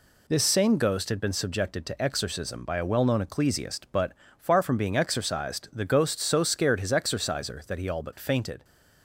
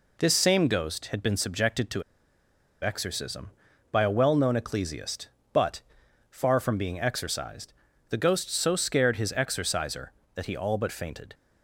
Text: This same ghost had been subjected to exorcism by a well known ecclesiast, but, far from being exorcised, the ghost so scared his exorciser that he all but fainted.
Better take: first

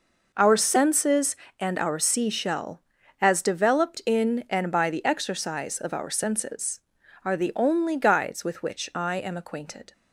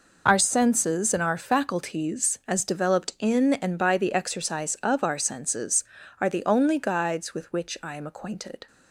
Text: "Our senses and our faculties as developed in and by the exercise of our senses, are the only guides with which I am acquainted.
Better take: second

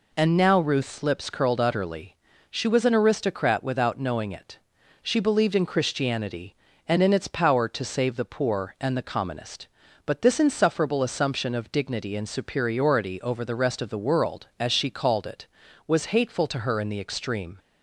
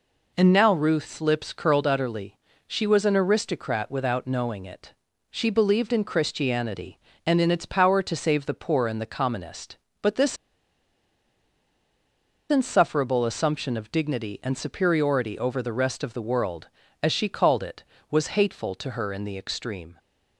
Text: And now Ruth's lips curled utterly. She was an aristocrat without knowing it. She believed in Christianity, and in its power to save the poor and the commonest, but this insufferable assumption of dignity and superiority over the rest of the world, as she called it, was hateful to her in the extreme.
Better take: first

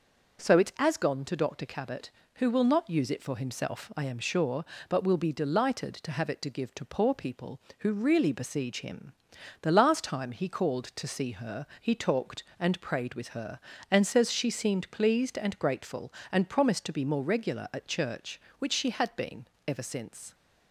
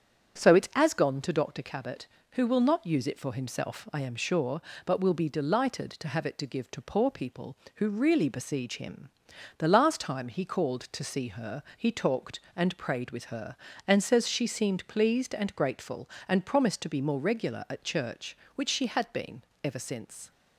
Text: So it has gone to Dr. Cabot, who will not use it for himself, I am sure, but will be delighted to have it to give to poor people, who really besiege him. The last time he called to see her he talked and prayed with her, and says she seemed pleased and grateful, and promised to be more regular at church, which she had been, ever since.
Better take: first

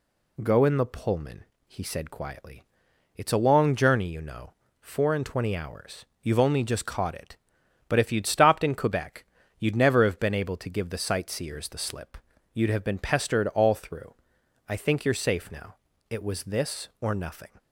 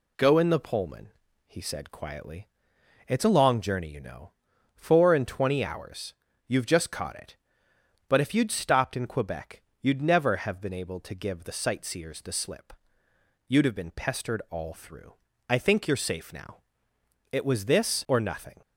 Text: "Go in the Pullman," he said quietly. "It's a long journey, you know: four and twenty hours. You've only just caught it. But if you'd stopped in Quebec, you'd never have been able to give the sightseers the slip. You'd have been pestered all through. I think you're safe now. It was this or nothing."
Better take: first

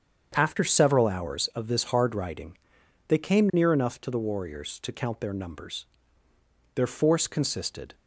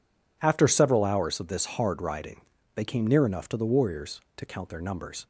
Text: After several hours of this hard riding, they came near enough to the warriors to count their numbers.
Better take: second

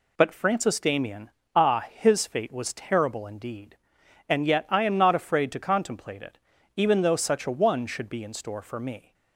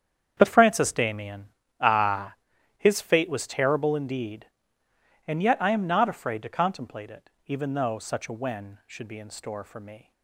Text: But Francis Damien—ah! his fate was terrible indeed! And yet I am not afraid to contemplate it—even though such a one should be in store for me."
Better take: first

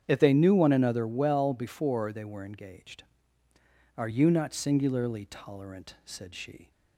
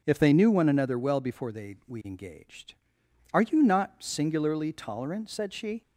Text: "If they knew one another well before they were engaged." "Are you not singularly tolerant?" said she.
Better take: first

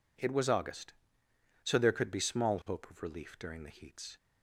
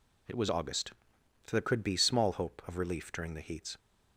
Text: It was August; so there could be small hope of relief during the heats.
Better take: neither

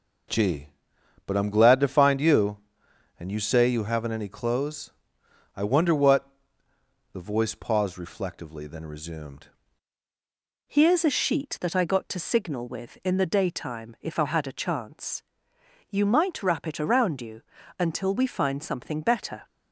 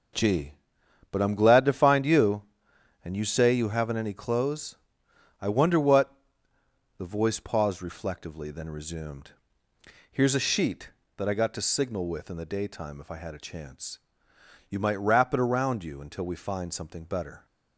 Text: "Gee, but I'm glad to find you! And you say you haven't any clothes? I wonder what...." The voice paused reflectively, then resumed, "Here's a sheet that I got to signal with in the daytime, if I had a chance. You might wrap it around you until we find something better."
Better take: second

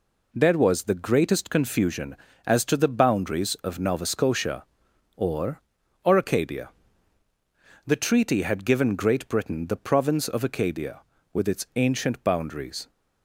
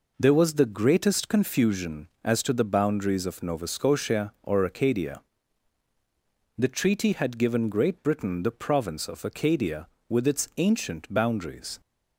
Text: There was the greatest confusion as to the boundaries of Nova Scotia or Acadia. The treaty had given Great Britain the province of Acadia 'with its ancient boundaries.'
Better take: second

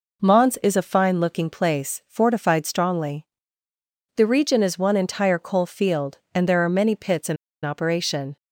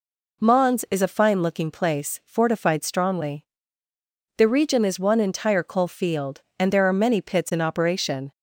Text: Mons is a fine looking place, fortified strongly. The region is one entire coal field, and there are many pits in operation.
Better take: second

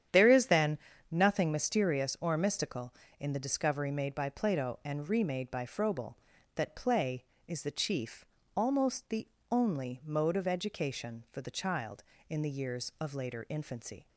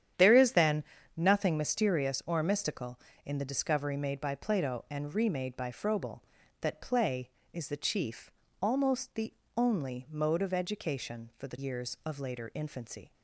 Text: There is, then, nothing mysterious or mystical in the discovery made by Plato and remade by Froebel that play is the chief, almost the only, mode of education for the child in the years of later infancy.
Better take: first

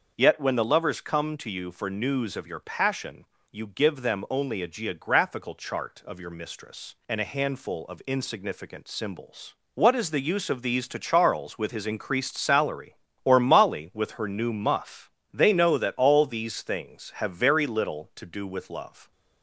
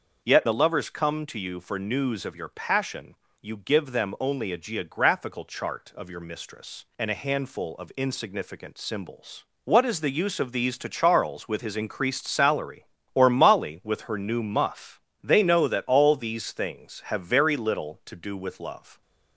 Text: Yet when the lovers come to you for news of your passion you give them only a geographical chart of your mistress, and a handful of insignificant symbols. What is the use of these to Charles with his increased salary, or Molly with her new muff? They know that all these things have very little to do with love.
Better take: first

